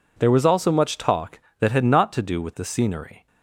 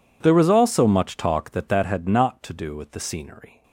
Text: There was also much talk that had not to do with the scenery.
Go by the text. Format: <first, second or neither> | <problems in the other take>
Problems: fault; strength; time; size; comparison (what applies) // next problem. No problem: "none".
first | says "that" twice; at 1.6 s